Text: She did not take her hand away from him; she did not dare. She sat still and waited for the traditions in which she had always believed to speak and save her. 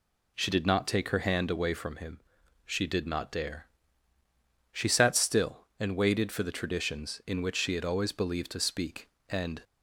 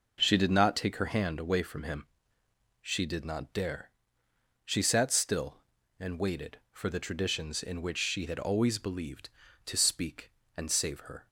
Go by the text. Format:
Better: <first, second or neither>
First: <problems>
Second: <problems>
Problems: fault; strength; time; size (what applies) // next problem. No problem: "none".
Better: second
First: stops before "save her"; at 9.6 s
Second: none